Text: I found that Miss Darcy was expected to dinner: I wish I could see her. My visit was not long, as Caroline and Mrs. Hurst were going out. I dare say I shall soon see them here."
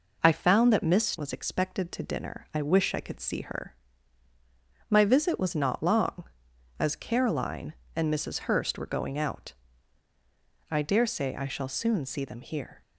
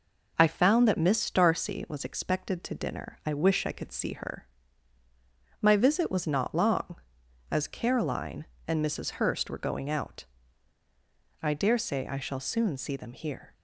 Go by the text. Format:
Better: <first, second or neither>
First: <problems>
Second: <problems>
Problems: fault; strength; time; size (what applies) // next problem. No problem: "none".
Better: second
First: skips "Darcy"; at 1.1 s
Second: none